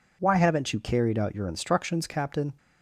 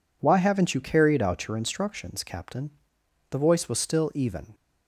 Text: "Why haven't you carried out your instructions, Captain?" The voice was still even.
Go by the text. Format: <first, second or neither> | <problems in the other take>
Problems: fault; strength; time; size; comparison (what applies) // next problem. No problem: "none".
second | stops before "The voice was still even"; at 2.5 s